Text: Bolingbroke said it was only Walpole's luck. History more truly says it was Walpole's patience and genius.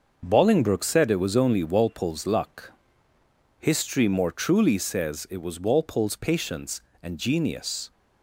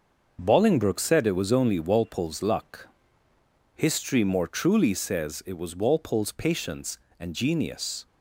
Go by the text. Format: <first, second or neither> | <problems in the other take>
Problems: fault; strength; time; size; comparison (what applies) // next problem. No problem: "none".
neither | starts louder than the rest; the same in both